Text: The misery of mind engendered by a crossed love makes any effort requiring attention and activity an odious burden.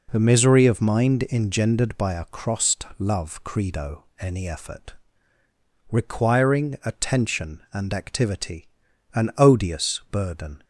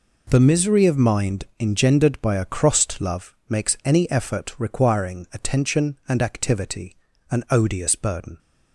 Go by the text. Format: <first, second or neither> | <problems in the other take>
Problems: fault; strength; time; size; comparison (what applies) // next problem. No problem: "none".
second | says "credo" for "makes"; at 3.4 s // pauses between "effort" and "requiring"; noticeable; at 4.9 s; 0.98 s long // pauses between "activity" and "an"; noticeable; at 8.6 s; 0.48 s long; slight in the second